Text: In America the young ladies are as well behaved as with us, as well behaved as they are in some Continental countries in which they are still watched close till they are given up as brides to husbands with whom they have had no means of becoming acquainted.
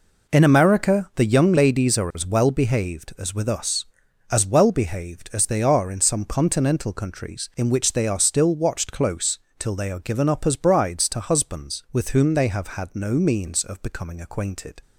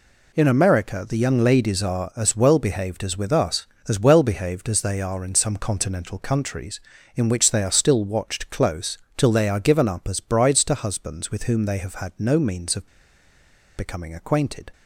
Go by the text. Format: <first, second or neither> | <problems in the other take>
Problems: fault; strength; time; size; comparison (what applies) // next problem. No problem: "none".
first | pauses between "close" and "till"; slight; at 8.9 s; 0.22 s long; slight in the first // pauses between "of" and "becoming"; noticeable; at 12.8 s; 0.91 s long